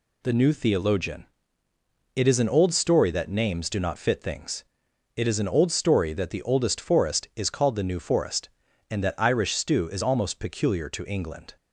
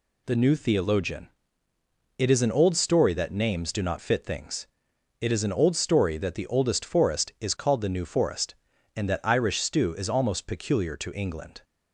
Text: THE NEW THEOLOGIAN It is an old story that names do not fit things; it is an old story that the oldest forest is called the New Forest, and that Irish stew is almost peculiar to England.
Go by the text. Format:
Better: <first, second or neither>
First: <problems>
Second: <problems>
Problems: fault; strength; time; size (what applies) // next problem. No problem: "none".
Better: neither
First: pauses between "THEOLOGIAN" and "It"; noticeable; at 1.2 s; 0.86 s long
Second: pauses between "THEOLOGIAN" and "It"; noticeable; at 1.3 s; 0.86 s long